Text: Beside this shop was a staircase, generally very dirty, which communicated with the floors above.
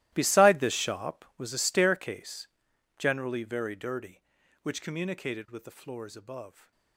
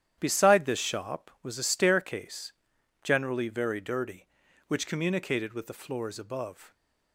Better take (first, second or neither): second